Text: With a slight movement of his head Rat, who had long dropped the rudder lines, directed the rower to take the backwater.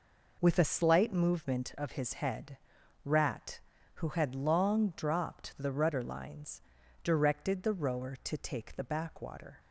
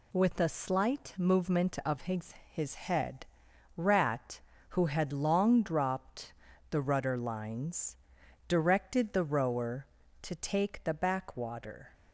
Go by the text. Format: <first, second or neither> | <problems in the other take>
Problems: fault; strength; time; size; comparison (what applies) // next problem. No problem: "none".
first | says "his" twice; at 2.4 s // pauses between "head" and "Rat"; noticeable; at 3.2 s; 0.52 s long; noticeable in the first // pauses between "dropped" and "the"; at 6.3 s; 0.38 s long